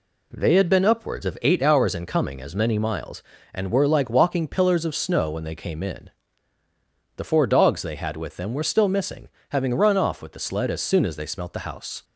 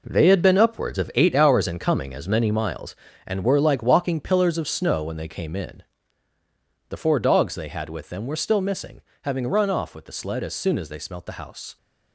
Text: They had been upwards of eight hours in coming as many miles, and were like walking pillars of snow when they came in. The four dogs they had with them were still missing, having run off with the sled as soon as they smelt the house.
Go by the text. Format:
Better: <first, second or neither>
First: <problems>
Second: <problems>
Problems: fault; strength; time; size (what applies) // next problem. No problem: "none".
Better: first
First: none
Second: gets quieter; strong; throughout; 9.5 dB